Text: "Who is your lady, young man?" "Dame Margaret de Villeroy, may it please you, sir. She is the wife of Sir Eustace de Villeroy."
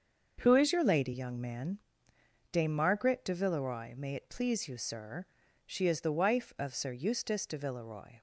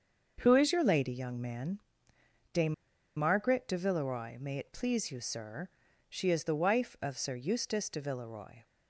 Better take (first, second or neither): first